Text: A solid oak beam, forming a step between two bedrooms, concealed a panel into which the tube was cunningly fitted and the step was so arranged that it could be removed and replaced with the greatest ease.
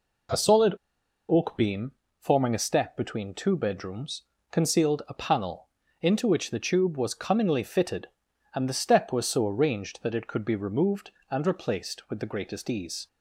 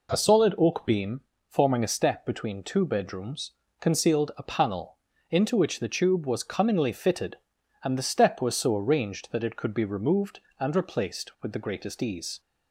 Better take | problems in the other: second | pauses between "solid" and "oak"; noticeable; at 0.7 s; 0.52 s long // pauses between "panel" and "into"; slight; at 5.6 s; 0.34 s long; slight in the second

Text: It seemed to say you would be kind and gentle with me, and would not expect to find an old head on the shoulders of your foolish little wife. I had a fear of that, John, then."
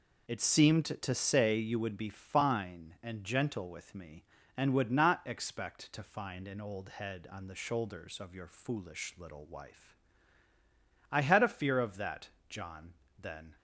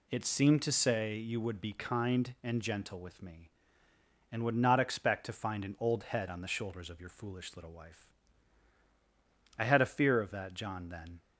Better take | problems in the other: second | says "fine" for "kind"; at 2.0 s

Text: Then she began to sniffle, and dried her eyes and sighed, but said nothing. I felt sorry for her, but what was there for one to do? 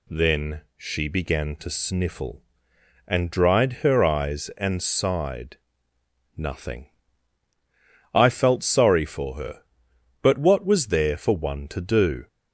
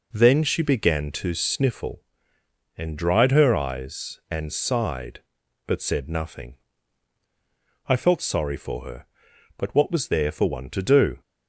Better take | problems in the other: second | pauses between "Then" and "she"; slight; at 0.6 s; 0.16 s long // skips "but said"; at 5.9 s

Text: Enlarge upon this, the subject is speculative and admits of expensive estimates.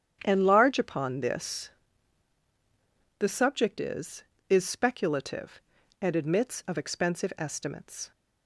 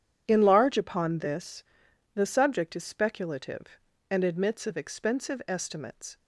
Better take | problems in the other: second | starts louder than the rest; strong; until 1.2 s; 9 dB // says "is" twice; at 4.4 s

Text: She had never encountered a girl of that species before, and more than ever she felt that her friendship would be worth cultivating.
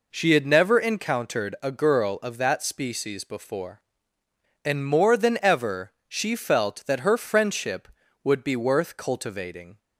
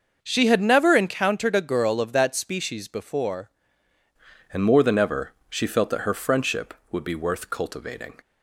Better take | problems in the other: first | starts louder than the rest; noticeable; until 1.2 s; 6 dB // changes voice at "and"; from 4.5 s on; 3.6 s long // pauses between "ever" and "she"; slight; at 5.3 s; 0.18 s long; slight in the first

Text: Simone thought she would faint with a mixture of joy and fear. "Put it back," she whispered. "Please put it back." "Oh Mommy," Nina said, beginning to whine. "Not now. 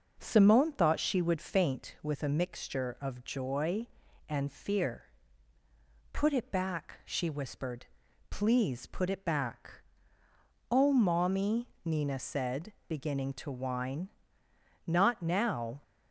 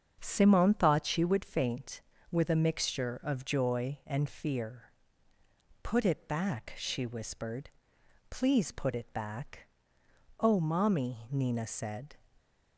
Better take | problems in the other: first | starts louder than the rest; until 1.2 s; 7 dB // stops before "beginning to whine Not now"; at 12.3 s

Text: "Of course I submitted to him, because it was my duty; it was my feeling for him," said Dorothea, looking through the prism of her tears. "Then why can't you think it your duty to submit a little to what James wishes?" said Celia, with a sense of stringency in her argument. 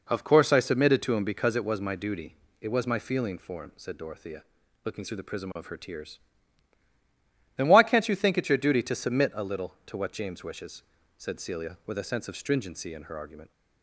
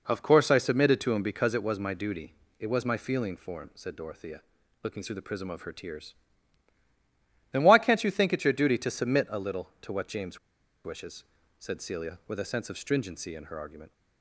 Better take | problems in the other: first | pauses between "James" and "wishes"; noticeable; at 10.3 s; 0.46 s long

